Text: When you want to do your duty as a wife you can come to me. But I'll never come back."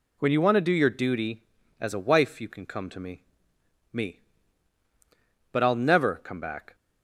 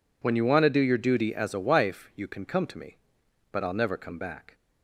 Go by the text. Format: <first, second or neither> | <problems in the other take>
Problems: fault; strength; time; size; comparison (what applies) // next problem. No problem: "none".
second | says "me" twice; at 3.9 s